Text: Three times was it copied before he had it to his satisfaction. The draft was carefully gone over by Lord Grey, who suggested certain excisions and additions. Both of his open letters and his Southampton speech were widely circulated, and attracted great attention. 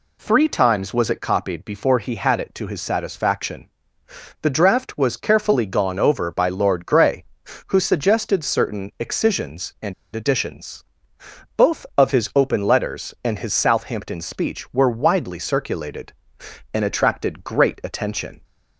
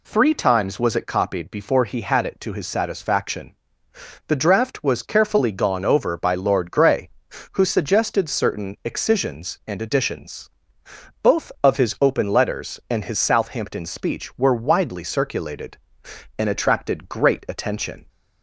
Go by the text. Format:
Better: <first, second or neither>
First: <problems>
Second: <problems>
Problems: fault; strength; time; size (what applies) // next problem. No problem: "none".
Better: second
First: pauses between "and" and "additions"; slight; at 9.9 s; 0.20 s long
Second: none